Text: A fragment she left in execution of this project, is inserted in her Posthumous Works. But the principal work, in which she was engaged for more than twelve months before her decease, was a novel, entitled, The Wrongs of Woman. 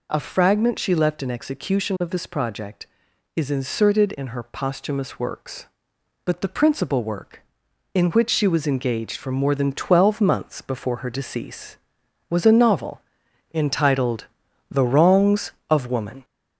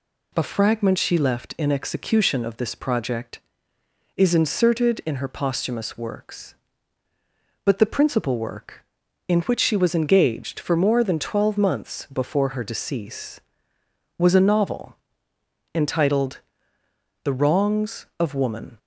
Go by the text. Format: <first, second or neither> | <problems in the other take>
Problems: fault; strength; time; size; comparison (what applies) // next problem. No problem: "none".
second | gets louder; throughout; 3.5 dB